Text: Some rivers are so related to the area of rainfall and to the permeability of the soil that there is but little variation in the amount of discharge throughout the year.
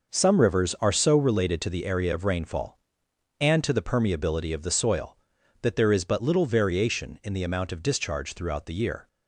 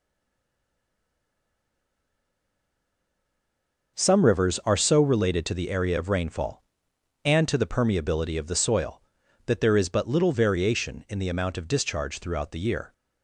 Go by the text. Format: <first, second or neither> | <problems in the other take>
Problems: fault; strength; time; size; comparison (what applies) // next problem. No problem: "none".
first | stays silent before the first word; strong; until 3.9 s; 3.9 s long